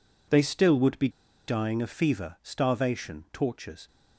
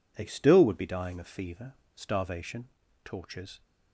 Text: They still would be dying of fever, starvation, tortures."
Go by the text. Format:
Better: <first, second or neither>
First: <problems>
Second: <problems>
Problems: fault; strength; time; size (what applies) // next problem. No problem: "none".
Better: second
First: pauses between "be" and "dying"; at 1.0 s; 0.39 s long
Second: none